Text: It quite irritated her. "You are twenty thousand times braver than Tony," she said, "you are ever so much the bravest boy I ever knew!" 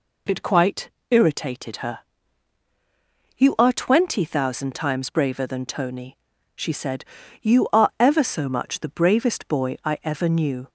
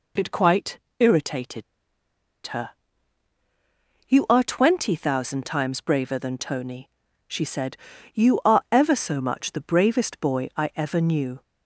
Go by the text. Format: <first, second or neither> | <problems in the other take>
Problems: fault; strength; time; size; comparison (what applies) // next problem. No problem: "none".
first | pauses between "quite" and "irritated"; slight; at 0.7 s; 0.20 s long; slight in the first // pauses between "irritated" and "her"; noticeable; at 1.6 s; 0.83 s long